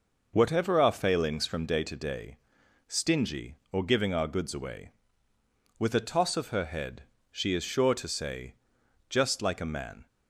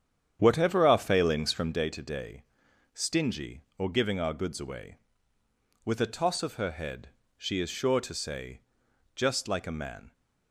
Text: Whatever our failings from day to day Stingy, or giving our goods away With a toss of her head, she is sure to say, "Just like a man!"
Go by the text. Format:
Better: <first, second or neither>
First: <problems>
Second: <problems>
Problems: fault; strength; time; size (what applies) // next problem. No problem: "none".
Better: first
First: pauses between "day" and "Stingy"; noticeable; at 2.3 s; 0.50 s long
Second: starts louder than the rest; strong; until 1.8 s; 9 dB // pauses between "day" and "Stingy"; noticeable; at 2.4 s; 0.50 s long